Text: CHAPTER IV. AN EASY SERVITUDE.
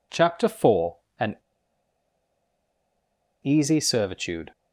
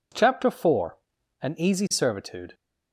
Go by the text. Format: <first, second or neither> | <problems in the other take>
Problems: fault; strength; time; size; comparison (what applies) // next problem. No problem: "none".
second | pauses between "AN" and "EASY"; strong; at 1.3 s; 2.0 s long